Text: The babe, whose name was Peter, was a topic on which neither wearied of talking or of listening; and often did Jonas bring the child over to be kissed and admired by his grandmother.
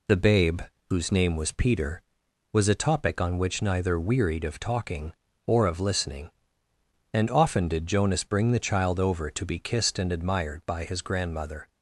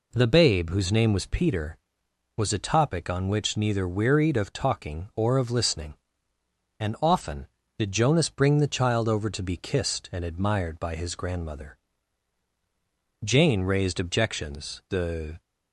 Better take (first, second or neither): first